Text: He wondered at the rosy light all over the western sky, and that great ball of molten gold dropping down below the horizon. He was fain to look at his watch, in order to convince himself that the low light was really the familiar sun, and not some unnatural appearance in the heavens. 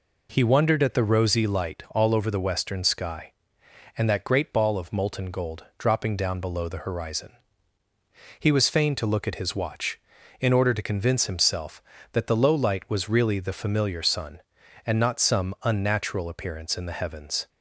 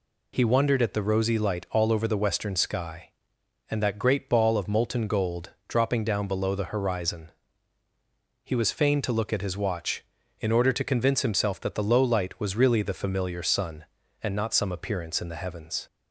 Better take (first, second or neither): first